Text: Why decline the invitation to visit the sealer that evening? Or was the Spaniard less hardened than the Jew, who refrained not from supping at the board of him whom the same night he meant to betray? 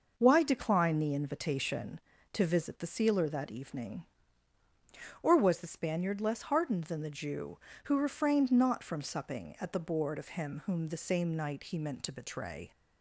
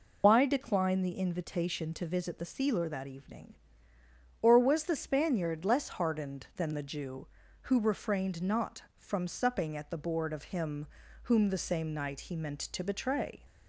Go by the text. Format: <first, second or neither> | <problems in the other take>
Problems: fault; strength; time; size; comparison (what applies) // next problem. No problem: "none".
first | loses the start of "Why"; at 0.2 s; 110 ms // pauses between "him" and "whom"; at 10.8 s; 0.38 s long